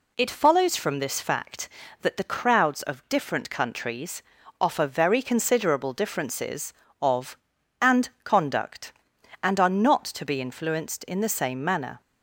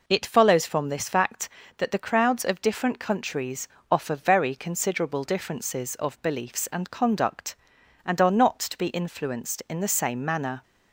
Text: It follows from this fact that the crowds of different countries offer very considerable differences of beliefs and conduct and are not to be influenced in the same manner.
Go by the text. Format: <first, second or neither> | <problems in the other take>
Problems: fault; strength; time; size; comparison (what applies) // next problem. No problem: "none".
second | pauses between "countries" and "offer"; at 4.2 s; 0.38 s long; slight in the second // skips "beliefs"; at 7.5 s